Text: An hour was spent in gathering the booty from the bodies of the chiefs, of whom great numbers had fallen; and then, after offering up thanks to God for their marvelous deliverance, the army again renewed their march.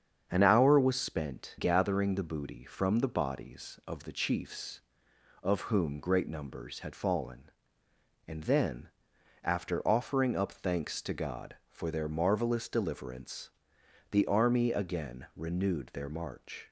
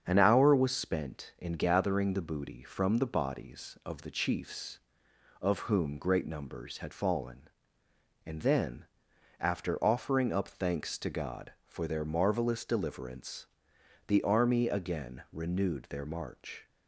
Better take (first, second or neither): second